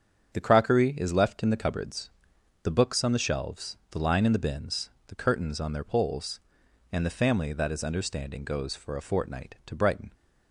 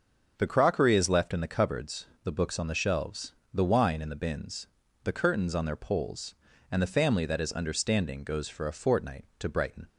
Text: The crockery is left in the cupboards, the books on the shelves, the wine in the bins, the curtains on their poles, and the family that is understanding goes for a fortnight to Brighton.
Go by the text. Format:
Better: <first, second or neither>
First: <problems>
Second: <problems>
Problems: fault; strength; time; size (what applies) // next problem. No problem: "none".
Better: second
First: starts louder than the rest; strong; until 1.3 s; 7.5 dB // says "line" for "wine"; at 3.9 s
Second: starts louder than the rest; noticeable; until 1.3 s; 6 dB